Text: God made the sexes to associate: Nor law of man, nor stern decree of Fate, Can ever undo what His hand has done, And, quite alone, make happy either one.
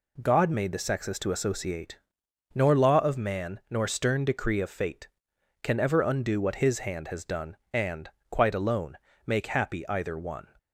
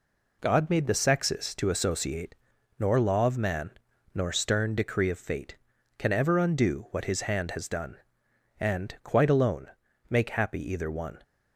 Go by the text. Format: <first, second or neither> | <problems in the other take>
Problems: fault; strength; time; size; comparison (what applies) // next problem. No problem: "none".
neither | none